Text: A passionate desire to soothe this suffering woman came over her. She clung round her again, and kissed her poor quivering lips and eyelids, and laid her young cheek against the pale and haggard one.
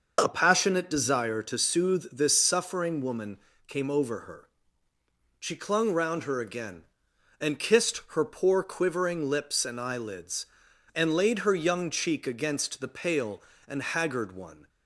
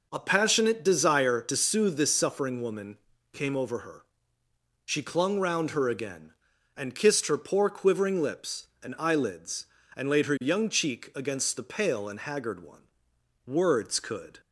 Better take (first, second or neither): first